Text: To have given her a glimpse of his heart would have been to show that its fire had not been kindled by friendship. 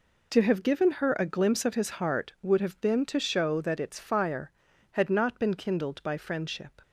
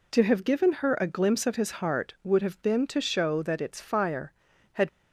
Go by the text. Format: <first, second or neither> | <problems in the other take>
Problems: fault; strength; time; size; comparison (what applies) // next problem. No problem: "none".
first | stops before "not been kindled by friendship"; at 4.8 s